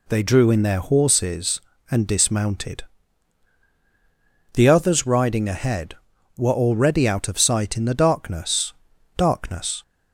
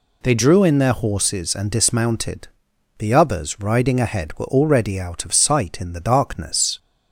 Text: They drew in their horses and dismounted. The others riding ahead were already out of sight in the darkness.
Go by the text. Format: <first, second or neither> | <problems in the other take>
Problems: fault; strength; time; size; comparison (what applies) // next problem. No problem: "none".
second | says "darkness" twice; at 9.1 s